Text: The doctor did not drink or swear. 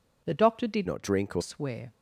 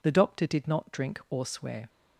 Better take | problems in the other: second | changes voice from "not" to "or"; from 0.8 to 1.4 s; 0.6 s long

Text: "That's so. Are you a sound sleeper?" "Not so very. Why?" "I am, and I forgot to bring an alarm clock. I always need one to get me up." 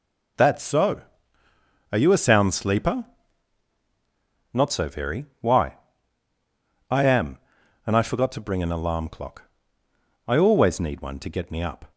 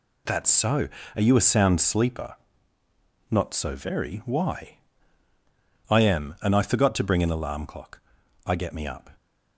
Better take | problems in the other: first | skips "always need one to"; at 8.5 s

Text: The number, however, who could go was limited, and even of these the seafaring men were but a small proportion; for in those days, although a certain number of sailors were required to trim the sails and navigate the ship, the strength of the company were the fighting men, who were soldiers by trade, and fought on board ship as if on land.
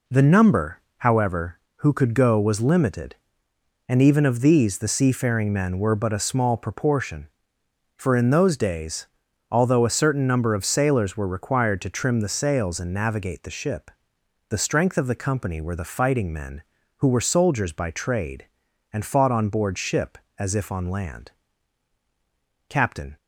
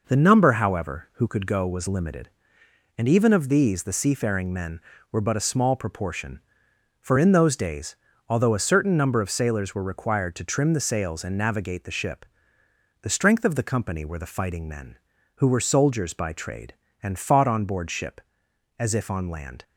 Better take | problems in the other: second | goes on to say "Captain"; slight; from 22.6 s on; 0.48 s long

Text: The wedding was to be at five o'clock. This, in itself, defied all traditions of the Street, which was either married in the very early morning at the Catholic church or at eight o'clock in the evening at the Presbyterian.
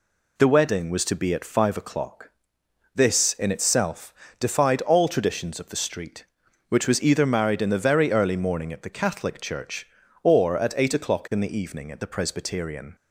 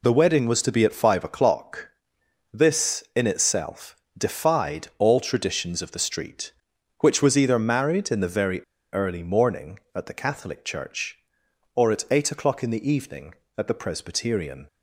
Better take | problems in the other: first | pauses between "very" and "early"; slight; at 8.6 s; 0.28 s long

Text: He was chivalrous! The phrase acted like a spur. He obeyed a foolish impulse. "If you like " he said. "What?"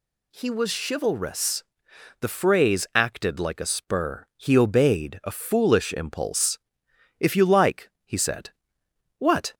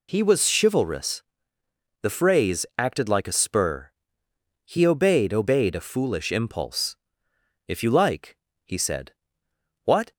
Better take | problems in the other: first | says "obeyed" twice; at 5.3 s

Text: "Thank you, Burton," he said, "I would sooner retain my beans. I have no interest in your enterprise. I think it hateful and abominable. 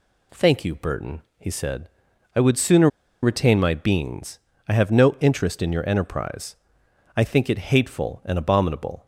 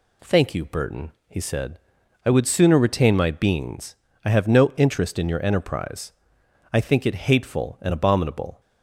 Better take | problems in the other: second | pauses between "sooner" and "retain"; slight; at 2.8 s; 0.34 s long

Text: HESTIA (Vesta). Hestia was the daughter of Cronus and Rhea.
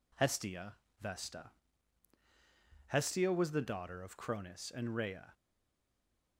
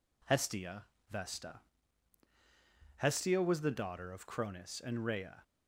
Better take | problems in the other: second | stays silent after the last word; from 5.3 s on; 1.0 s long

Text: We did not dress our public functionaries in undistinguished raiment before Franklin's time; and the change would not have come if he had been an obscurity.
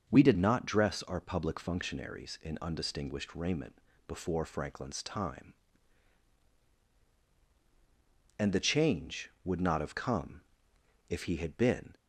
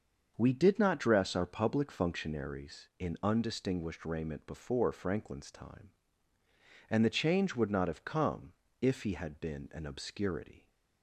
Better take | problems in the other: second | starts louder than the rest; until 1.1 s; 6.5 dB; also in the second // pauses between "raiment" and "before"; slight; at 3.8 s; 0.26 s long // pauses between "come" and "if"; noticeable; at 10.4 s; 0.66 s long; slight in the second // stops before "an obscurity"; at 11.9 s

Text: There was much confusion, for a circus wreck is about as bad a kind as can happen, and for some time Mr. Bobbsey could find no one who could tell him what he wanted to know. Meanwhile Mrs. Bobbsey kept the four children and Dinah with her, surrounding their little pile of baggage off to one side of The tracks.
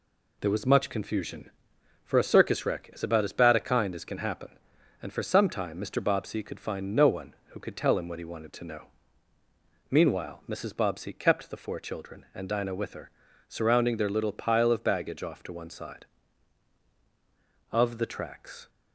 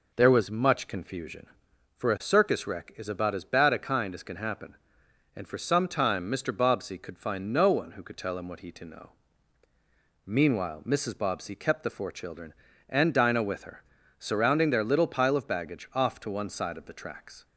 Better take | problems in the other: first | skips "wanted"; at 8.7 s

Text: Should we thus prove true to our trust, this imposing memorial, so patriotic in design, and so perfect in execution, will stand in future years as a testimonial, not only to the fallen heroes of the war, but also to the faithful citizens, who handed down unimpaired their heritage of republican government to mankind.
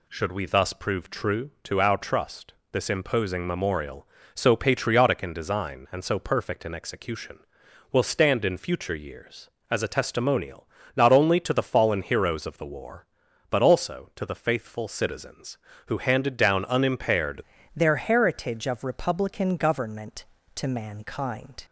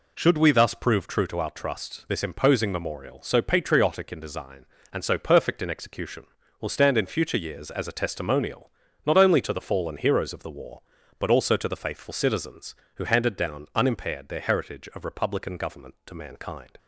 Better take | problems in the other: second | changes voice at "their"; from 17.7 s on; 3.9 s long

